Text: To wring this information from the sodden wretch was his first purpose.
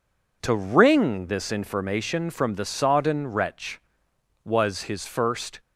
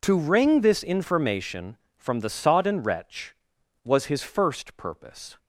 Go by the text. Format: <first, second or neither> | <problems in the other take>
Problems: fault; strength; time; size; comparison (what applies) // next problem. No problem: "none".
second | stops before "purpose"; at 5.5 s